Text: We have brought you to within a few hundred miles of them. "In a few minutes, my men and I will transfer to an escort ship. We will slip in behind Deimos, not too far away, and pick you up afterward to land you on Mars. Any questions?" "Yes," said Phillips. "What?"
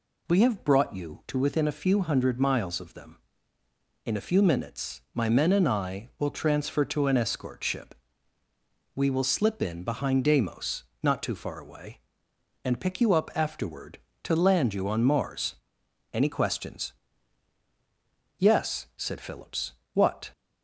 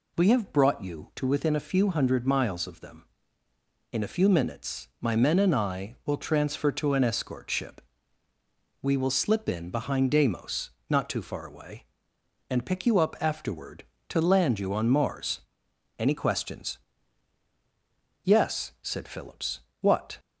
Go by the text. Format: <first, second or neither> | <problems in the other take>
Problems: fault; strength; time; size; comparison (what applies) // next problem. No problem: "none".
neither | none